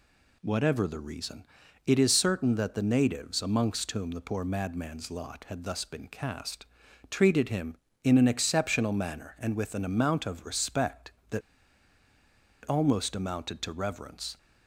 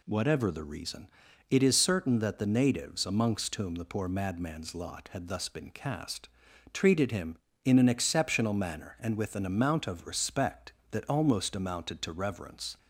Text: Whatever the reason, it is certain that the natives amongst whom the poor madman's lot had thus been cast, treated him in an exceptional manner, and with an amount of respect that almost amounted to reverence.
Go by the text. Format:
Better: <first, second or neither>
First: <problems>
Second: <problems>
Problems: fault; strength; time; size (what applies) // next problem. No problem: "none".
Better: second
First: pauses between "that" and "almost"; strong; at 11.4 s; 1.2 s long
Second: none